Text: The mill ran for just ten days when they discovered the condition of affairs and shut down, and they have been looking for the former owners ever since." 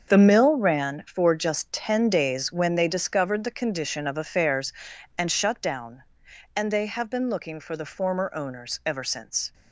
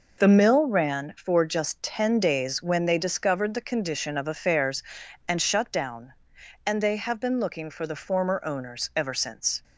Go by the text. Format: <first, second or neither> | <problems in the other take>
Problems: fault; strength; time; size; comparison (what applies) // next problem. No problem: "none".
second | gets quieter; strong; throughout; 10 dB